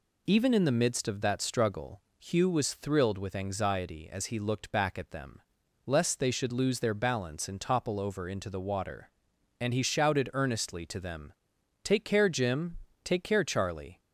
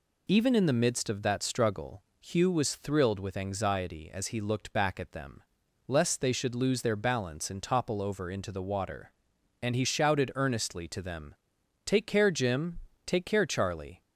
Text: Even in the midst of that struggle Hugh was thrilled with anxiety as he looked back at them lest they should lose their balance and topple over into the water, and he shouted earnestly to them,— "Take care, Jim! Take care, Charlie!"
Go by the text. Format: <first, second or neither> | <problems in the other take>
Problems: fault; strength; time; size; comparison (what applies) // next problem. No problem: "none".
neither | pauses between "struggle" and "Hugh"; slight; the same in both // pauses between "them" and "lest"; noticeable; the same in both